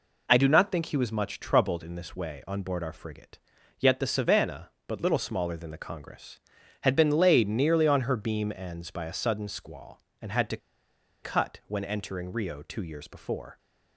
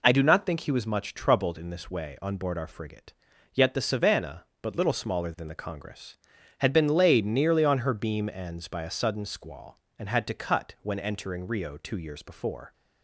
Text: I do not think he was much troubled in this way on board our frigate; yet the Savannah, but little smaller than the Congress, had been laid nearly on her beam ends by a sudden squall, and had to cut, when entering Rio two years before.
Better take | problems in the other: second | pauses between "to" and "cut"; noticeable; at 10.5 s; 0.65 s long

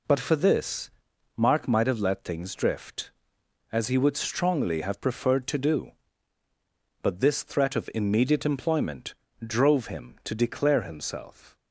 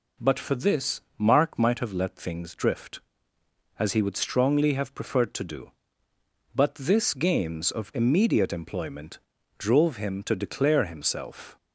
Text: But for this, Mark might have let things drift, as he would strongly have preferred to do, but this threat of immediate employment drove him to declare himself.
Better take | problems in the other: first | says "games" for "threat"; at 7.1 s // pauses between "employment" and "drove"; at 9.1 s; 0.40 s long; slight in the first

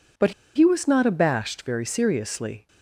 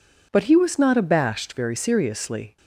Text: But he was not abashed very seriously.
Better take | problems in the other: second | pauses between "But" and "he"; slight; at 0.3 s; 0.23 s long

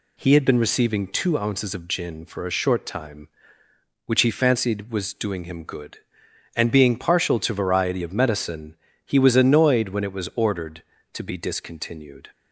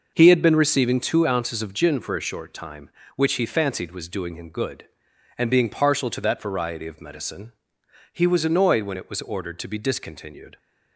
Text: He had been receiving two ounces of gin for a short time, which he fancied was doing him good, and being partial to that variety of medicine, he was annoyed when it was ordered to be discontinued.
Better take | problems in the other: second | skips "that"; at 7.5 s

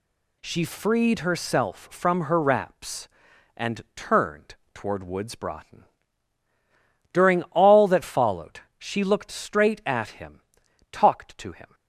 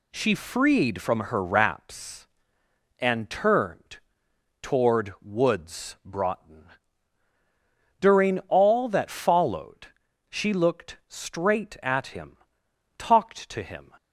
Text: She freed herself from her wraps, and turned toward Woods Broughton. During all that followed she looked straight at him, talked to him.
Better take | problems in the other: first | skips "herself"; at 1.0 s // pauses between "turned" and "toward"; noticeable; at 3.9 s; 0.62 s long; slight in the first // pauses between "followed" and "she"; at 9.8 s; 0.44 s long; slight in the first

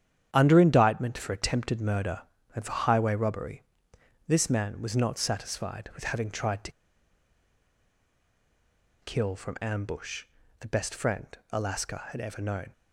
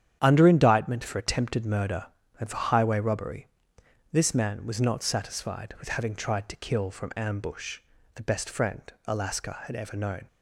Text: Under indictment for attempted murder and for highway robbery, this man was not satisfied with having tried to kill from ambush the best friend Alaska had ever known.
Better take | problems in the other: second | starts louder than the rest; strong; until 1.3 s; 9.5 dB; strong in the second // pauses between "to" and "kill"; strong; at 6.7 s; 2.3 s long // pauses between "ambush" and "the"; slight; at 10.2 s; 0.36 s long; slight in the second // pauses between "friend" and "Alaska"; slight; at 11.2 s; 0.26 s long; slight in the second

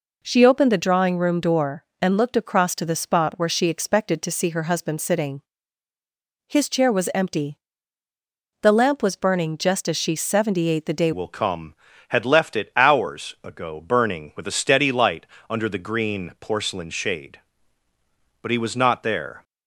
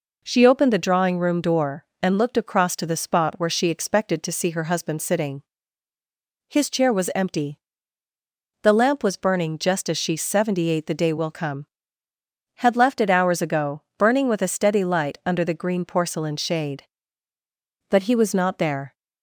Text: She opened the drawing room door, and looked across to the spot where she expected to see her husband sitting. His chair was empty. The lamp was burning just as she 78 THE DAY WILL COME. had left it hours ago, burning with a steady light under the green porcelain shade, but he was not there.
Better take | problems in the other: second | changes voice at "WILL"; from 11.1 s on; 8.3 s long // pauses between "light" and "under"; slight; at 15.2 s; 0.24 s long

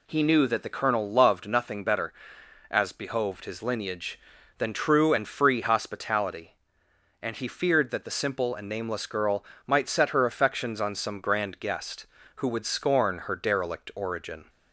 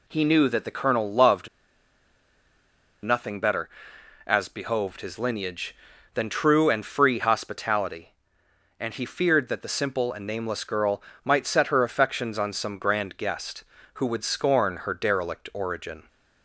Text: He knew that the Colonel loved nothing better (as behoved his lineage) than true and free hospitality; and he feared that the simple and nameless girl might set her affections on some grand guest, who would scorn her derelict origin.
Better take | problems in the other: first | pauses between "loved" and "nothing"; strong; at 1.4 s; 1.5 s long // pauses between "girl" and "might"; slight; at 11.0 s; 0.20 s long; slight in the first

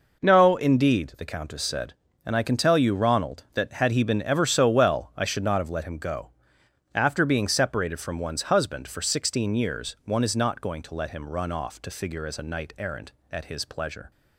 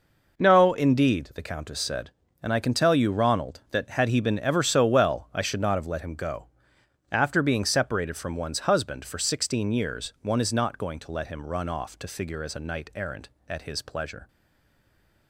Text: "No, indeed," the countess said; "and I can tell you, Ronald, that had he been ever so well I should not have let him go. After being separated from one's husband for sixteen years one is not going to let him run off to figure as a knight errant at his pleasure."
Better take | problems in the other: first | stays silent after the last word; from 14.2 s on; 1.0 s long

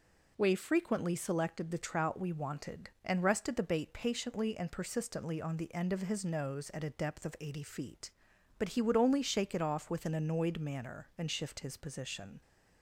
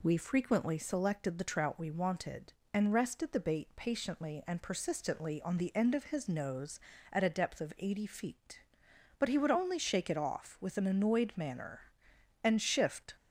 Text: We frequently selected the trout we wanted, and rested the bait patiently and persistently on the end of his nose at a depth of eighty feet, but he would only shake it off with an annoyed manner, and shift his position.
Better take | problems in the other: first | stops before "his position"; at 13.1 s

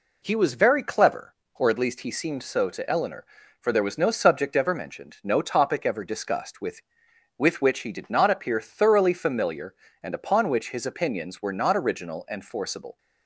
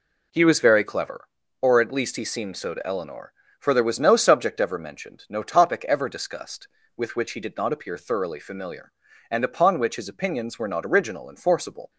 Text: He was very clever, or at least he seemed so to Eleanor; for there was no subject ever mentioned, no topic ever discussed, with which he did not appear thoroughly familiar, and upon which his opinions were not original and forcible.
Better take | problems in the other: second | says "with" twice; at 7.3 s

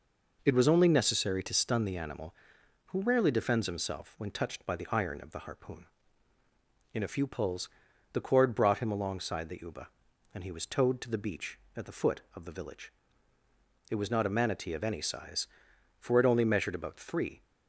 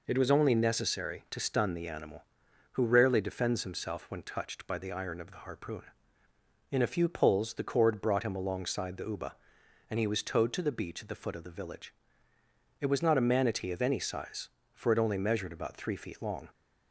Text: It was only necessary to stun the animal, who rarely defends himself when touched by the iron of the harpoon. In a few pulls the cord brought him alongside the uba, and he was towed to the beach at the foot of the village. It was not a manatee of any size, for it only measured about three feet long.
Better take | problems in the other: second | pauses between "pulls" and "the"; at 7.6 s; 0.44 s long // stops before "feet long"; at 17.4 s

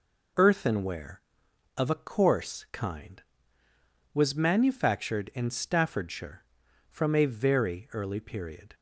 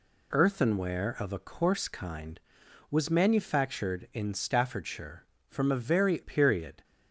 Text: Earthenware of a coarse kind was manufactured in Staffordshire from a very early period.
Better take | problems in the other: first | skips "early"; at 6.2 s

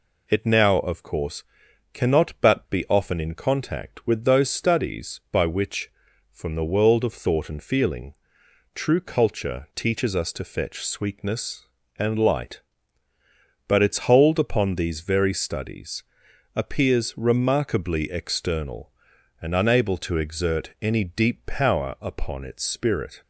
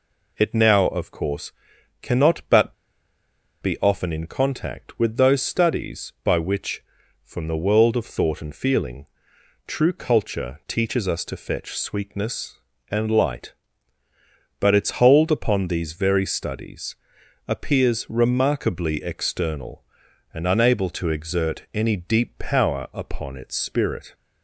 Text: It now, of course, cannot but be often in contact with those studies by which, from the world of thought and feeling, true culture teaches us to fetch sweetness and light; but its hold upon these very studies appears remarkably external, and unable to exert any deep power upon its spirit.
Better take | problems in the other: first | pauses between "but" and "be"; noticeable; at 2.7 s; 0.87 s long // pauses between "studies" and "appears"; noticeable; at 16.9 s; 0.52 s long; noticeable in the first

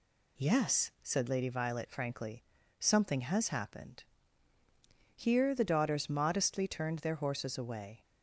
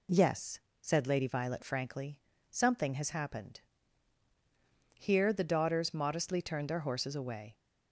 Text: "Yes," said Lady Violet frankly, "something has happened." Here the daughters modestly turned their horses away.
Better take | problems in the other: neither | none

